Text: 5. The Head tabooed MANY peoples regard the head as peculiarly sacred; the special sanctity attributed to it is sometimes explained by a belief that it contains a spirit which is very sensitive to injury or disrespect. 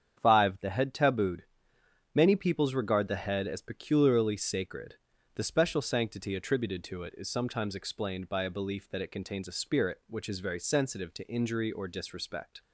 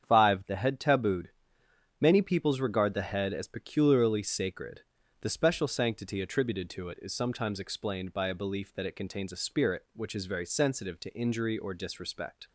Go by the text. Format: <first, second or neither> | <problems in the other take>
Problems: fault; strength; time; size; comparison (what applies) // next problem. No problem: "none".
neither | starts louder than the rest; strong; the same in both // pauses between "tabooed" and "MANY"; noticeable; the same in both